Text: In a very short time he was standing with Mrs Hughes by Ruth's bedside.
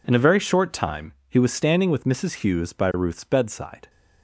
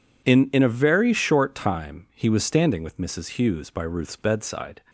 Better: first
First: none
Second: says "In" twice; at 0.5 s

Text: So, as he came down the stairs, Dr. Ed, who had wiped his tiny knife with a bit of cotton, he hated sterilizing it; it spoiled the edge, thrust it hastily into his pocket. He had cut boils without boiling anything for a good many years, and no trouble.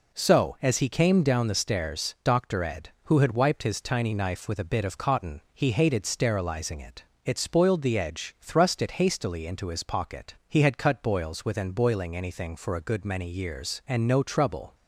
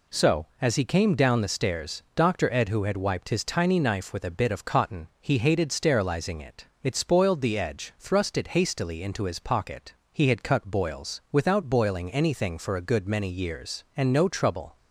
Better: second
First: says "within" for "without"; at 11.4 s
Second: none

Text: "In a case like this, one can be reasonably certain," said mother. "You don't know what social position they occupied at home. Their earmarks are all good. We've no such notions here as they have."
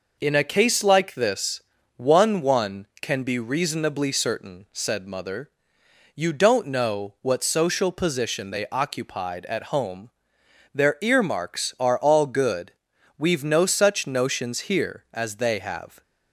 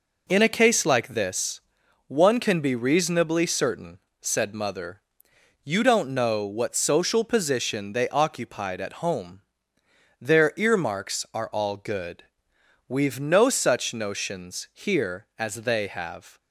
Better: second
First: says "one" twice; at 2.4 s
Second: none

